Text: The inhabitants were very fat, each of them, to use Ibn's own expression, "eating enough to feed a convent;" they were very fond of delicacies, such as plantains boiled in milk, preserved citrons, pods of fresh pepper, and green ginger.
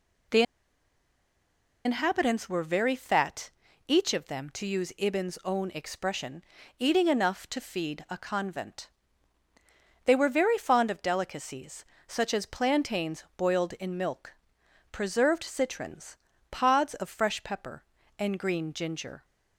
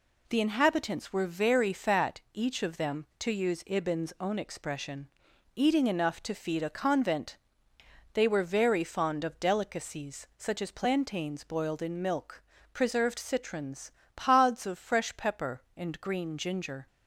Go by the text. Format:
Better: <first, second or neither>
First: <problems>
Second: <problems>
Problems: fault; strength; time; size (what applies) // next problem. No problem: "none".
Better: second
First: pauses between "The" and "inhabitants"; strong; at 0.4 s; 1.4 s long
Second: none